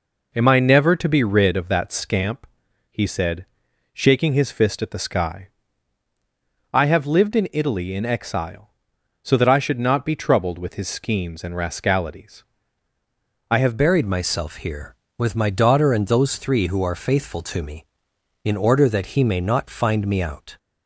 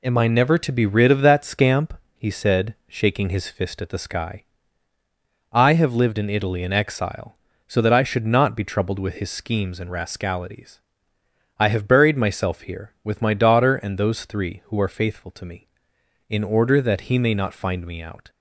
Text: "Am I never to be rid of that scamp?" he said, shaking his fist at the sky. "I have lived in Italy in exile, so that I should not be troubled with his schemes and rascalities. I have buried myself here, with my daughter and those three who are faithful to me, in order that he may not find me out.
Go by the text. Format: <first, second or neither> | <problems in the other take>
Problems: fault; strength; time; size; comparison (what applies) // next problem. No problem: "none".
second | changes voice at "buried"; from 13.7 s on; 6.8 s long